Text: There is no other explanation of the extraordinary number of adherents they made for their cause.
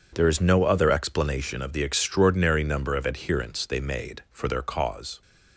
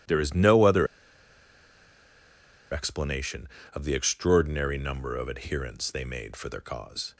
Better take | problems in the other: first | pauses between "other" and "explanation"; strong; at 0.8 s; 1.8 s long

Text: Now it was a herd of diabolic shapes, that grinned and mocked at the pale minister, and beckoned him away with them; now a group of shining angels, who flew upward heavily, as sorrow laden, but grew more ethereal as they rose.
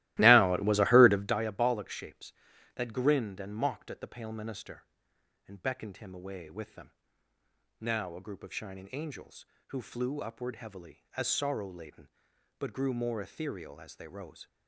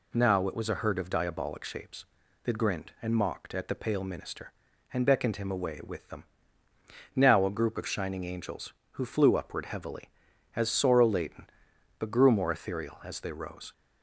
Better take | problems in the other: second | starts louder than the rest; strong; until 1.4 s; 16.5 dB

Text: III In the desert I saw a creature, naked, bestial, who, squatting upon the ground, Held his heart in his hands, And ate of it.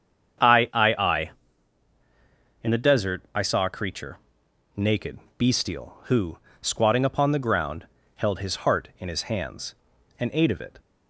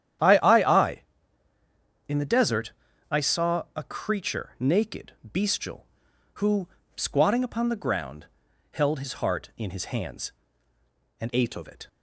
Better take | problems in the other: first | starts louder than the rest; strong; until 2.3 s; 10 dB; strong in the first // pauses between "desert" and "I"; slight; at 2.7 s; 0.36 s long // changes voice from "ate" to "of"; from 11.3 to 11.6 s; 0.3 s long

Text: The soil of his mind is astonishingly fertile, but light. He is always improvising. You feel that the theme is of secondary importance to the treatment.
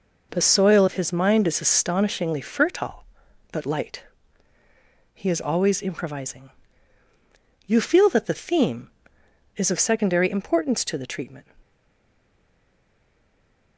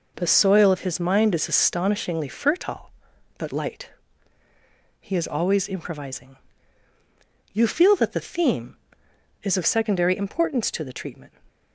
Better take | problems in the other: second | stays silent after the last word; from 11.6 s on; 2.1 s long

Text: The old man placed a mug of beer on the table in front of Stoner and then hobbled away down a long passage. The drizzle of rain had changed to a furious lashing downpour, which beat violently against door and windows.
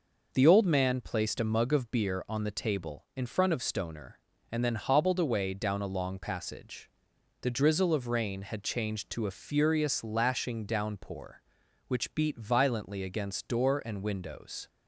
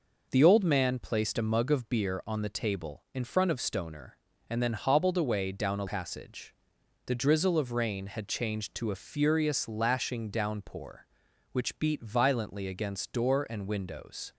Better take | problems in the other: first | skips "long"; at 5.8 s

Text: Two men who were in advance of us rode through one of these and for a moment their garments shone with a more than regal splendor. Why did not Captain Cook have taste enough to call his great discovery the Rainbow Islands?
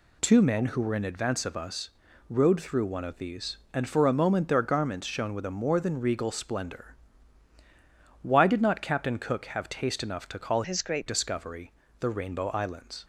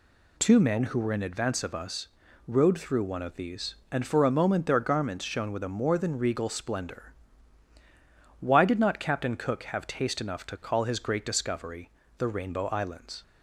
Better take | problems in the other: second | pauses between "us" and "rode"; at 1.9 s; 0.38 s long; also in the second // changes voice from "his" to "great"; from 10.6 to 11.0 s; 0.4 s long // pauses between "discovery" and "the"; slight; at 11.7 s; 0.26 s long; slight in the second

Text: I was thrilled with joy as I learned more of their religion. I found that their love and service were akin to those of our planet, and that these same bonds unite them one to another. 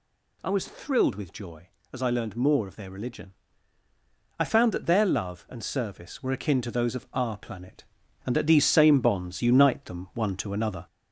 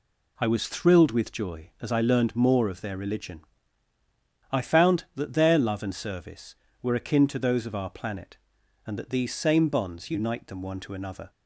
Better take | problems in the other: second | gets louder; slight; throughout; 2.5 dB

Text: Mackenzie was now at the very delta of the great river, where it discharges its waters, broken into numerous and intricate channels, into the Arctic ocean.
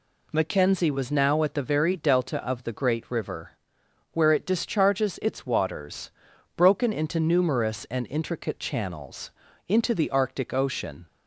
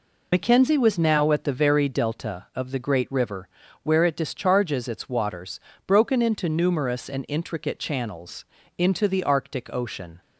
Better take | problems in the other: first | loses the start of "Mackenzie"; at 0.3 s; 60 ms

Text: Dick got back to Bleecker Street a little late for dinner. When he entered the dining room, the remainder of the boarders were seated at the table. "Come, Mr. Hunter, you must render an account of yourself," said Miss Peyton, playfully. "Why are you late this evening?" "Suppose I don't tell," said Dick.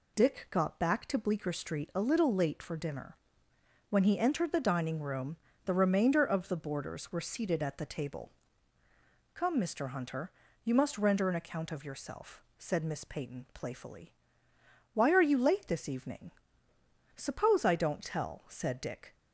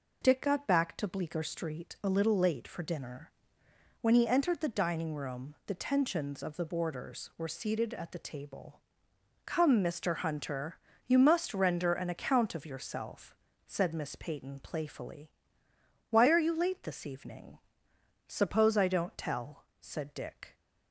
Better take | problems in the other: first | says "tensions" for "remainder"; at 5.7 s

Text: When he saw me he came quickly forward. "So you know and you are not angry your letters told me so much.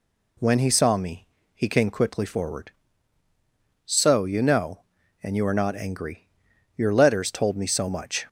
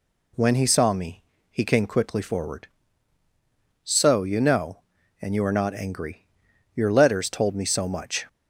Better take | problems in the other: neither | pauses between "me" and "he"; slight; the same in both // pauses between "angry" and "your"; noticeable; the same in both

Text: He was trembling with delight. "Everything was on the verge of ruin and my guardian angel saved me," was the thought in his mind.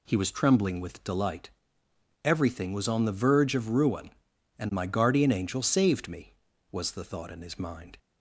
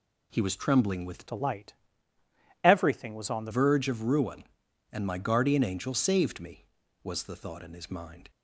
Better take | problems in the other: first | changes voice from "delight" to "the"; from 1.2 to 3.5 s; 2.3 s long

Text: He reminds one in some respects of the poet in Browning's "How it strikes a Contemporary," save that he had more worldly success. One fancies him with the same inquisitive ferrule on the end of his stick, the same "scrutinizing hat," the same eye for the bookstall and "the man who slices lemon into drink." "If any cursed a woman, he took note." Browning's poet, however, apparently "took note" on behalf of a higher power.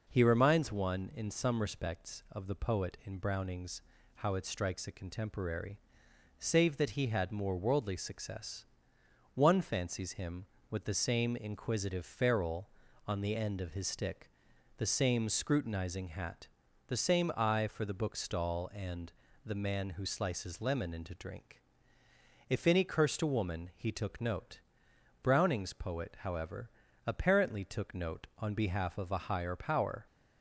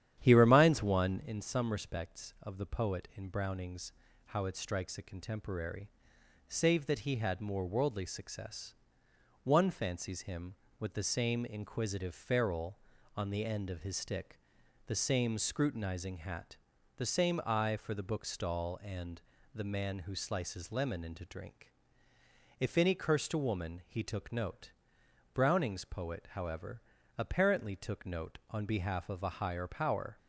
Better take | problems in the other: first | starts louder than the rest; strong; until 1.3 s; 10.5 dB // pauses between "Browning's" and "How"; slight; at 3.9 s; 0.34 s long; slight in the first // pauses between "and" and "the"; slight; at 19.2 s; 0.32 s long; slight in the first

